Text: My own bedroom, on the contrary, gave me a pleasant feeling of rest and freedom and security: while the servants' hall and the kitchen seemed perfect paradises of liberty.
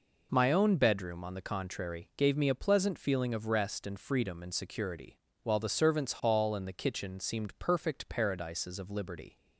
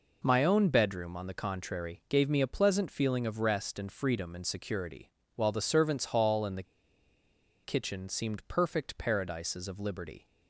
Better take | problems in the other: first | pauses between "the" and "kitchen"; at 6.6 s; 1.0 s long

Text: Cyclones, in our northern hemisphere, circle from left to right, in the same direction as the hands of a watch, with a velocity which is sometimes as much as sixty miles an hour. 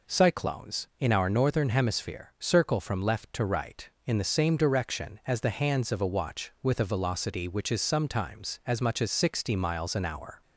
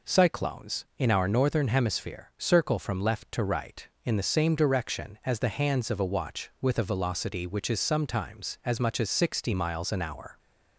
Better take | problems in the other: neither | none

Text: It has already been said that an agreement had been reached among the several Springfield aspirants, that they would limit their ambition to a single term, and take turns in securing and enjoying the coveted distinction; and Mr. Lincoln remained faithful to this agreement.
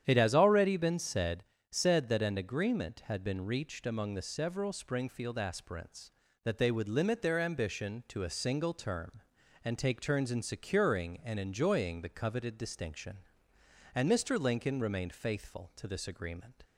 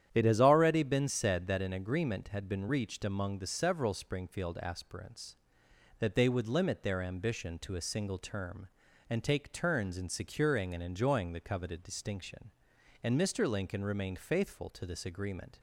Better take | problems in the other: second | starts louder than the rest; strong; until 1.0 s; 9.5 dB; strong in the second // says "said" twice; at 1.7 s

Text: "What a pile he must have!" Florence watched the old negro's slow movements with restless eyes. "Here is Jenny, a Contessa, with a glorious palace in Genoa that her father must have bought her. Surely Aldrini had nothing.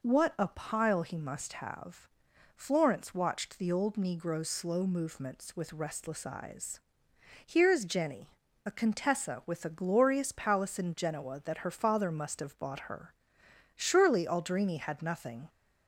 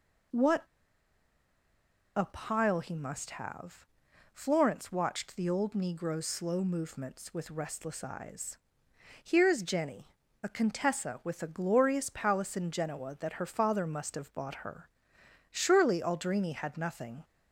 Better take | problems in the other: first | pauses between "What" and "a"; strong; at 0.6 s; 1.5 s long

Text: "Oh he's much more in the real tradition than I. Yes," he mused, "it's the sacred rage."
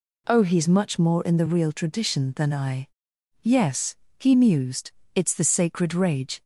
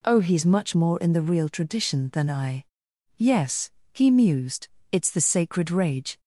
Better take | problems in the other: neither | none

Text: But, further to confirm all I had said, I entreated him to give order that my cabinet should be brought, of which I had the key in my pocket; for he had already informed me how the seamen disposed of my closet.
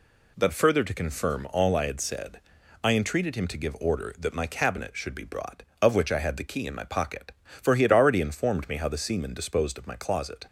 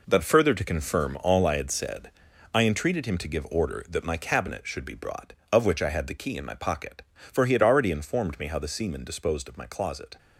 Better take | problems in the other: first | gets quieter; strong; throughout; 8.5 dB

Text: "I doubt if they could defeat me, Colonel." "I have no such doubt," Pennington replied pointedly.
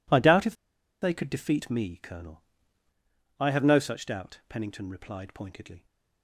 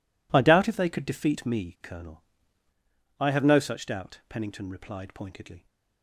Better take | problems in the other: second | pauses between "if" and "they"; noticeable; at 0.5 s; 0.47 s long

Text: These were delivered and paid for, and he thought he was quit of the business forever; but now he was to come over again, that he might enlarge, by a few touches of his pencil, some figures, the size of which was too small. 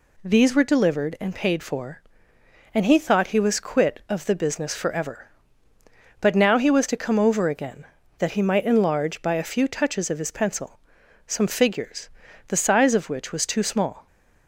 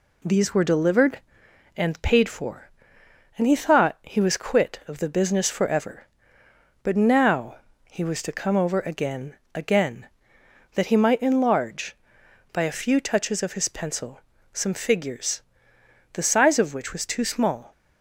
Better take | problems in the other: first | pauses between "now" and "he"; slight; at 7.5 s; 0.34 s long // says "again" twice; at 9.5 s

